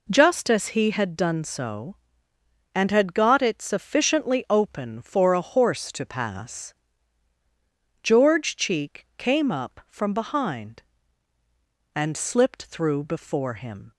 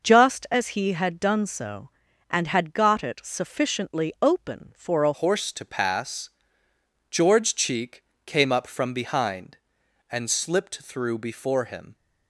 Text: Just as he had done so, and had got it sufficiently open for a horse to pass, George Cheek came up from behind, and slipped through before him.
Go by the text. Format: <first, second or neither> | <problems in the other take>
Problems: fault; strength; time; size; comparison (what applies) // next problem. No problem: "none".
first | changes voice at "horse"; from 5.1 s on; 6.8 s long // pauses between "Cheek" and "came"; slight; at 8.0 s; 0.22 s long